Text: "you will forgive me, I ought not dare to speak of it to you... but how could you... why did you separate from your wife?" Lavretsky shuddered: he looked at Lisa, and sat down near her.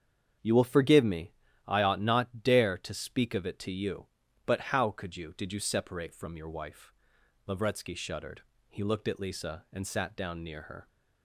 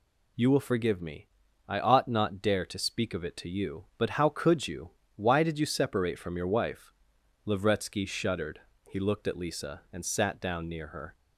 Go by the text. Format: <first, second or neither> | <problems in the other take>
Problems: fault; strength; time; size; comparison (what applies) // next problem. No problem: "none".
second | starts louder than the rest; strong; until 1.7 s; 7.5 dB // skips "why"; at 5.3 s